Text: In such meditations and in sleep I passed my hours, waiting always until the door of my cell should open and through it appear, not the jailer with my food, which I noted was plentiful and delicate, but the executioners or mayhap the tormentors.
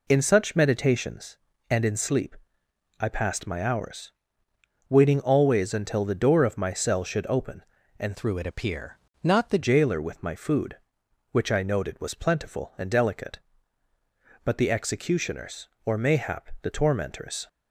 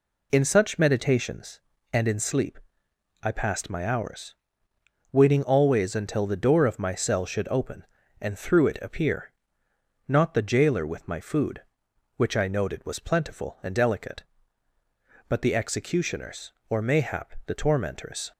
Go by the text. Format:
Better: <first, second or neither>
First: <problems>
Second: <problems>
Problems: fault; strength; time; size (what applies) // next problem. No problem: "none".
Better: second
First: pauses between "sleep" and "I"; noticeable; at 2.3 s; 0.60 s long // changes voice from "through" to "the"; from 8.1 to 9.5 s; 1.4 s long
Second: pauses between "sleep" and "I"; noticeable; at 2.5 s; 0.60 s long